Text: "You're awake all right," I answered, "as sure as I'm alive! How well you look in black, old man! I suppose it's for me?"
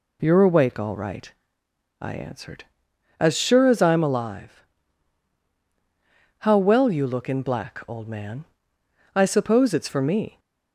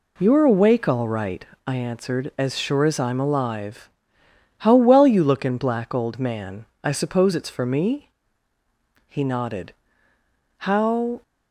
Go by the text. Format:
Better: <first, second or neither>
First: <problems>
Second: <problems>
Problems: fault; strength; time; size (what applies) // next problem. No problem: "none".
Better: first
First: none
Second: goes on to say "He nodded How"; strong; from 9.0 s on; 2.1 s long